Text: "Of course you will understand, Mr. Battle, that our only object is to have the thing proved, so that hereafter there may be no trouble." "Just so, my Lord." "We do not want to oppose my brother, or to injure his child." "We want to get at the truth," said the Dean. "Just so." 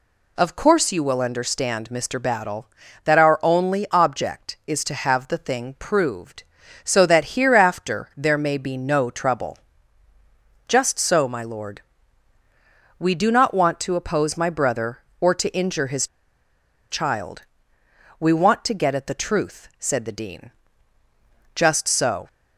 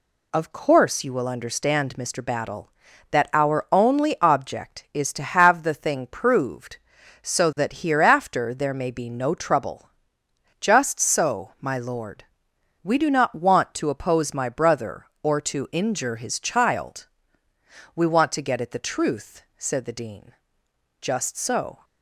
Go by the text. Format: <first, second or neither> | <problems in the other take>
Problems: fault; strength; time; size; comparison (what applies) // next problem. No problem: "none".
second | pauses between "his" and "child"; noticeable; at 16.0 s; 0.83 s long